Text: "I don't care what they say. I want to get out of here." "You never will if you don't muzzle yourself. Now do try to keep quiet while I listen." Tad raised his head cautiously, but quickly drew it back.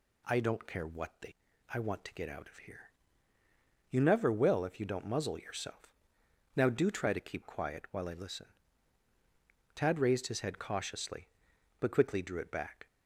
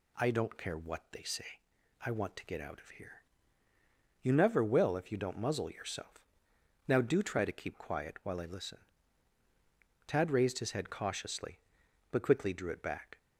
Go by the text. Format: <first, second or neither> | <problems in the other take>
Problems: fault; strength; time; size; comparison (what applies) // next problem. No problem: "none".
second | skips "say"; at 1.5 s